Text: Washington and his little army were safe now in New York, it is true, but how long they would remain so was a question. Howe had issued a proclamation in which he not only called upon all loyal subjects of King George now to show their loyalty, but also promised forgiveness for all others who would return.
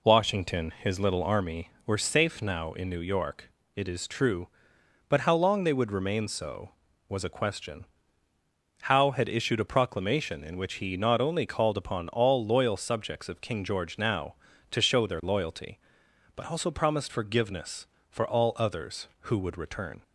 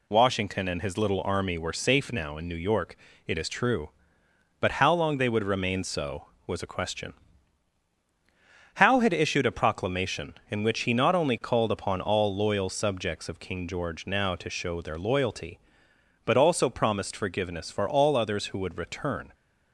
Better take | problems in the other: second | skips "and"; at 0.7 s

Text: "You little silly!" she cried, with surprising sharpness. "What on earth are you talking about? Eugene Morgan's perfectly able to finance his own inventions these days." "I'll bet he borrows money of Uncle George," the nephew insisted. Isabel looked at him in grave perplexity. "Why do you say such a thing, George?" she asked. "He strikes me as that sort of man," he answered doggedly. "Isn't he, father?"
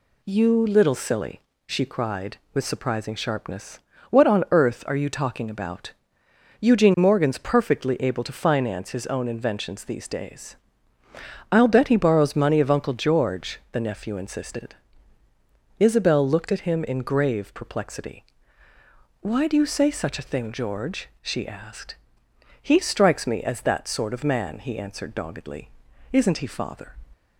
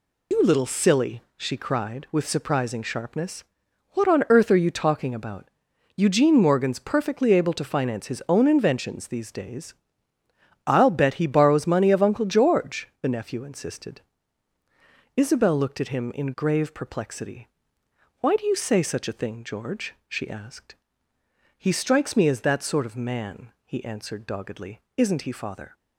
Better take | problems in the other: first | loses the start of "You"; at 0.3 s; 95 ms

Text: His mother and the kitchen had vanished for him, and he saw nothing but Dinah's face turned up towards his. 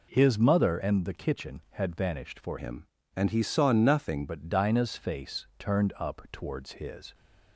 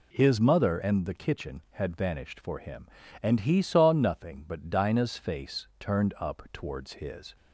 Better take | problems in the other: second | changes voice from "him" to "nothing"; from 2.5 to 4.2 s; 1.7 s long

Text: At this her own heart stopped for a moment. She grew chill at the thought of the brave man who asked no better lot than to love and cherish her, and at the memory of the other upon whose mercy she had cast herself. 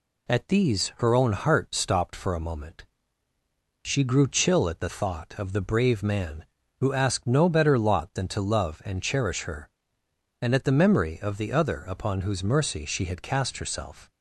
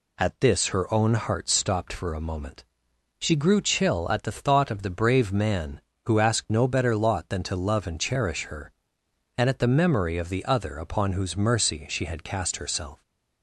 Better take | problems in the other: second | says "these" for "this"; at 0.4 s

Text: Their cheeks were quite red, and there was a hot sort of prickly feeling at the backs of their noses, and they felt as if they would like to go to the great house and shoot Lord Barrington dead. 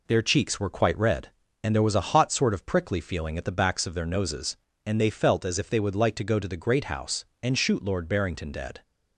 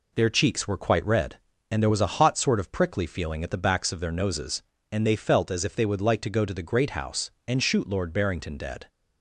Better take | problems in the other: neither | none

